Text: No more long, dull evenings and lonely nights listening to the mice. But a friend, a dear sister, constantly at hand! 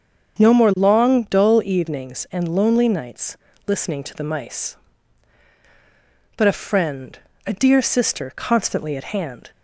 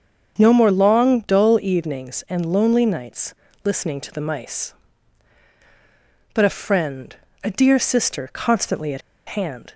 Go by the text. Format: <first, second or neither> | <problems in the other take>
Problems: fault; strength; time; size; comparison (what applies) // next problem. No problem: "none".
first | starts louder than the rest; until 1.3 s; 7 dB; also in the first // pauses between "nights" and "listening"; slight; at 3.3 s; 0.32 s long; slight in the first // pauses between "at" and "hand"; slight; at 9.0 s; 0.27 s long